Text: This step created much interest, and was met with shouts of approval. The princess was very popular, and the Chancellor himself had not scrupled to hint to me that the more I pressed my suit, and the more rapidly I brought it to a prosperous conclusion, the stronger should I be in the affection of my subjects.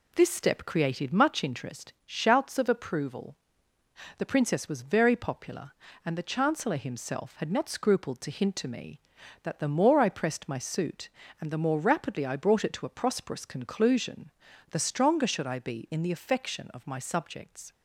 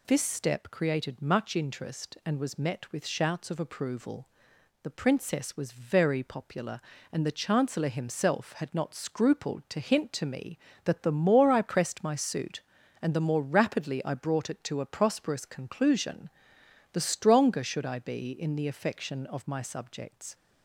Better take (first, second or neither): second